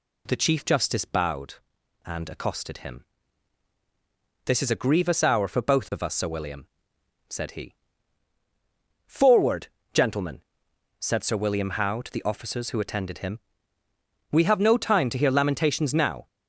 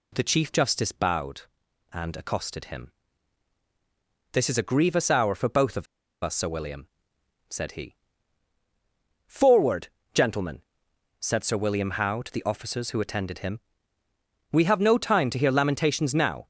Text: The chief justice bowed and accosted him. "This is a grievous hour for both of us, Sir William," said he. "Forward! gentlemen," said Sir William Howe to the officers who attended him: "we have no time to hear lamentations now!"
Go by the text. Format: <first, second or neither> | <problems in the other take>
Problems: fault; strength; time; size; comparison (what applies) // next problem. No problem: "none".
first | pauses between "of" and "us"; at 5.8 s; 0.37 s long